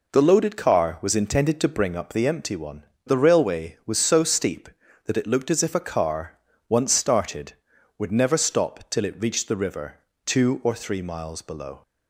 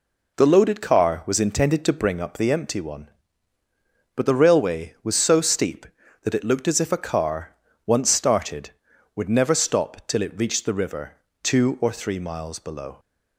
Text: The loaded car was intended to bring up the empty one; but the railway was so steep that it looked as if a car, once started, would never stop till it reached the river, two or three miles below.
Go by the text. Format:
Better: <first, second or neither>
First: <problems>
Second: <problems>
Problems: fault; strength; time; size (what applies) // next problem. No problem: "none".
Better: second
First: skips "but"; at 2.9 s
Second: none